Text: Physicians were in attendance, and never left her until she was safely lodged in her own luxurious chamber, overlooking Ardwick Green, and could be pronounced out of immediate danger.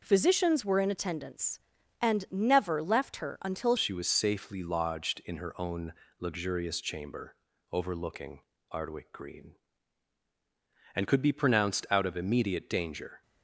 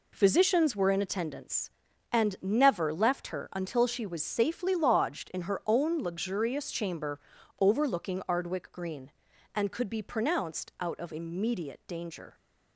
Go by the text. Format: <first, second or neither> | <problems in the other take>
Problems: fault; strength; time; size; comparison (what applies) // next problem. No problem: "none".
second | changes voice at "she"; from 3.7 s on; 9.5 s long // pauses between "own" and "luxurious"; slight; at 5.9 s; 0.26 s long // pauses between "overlooking" and "Ardwick"; slight; at 8.4 s; 0.28 s long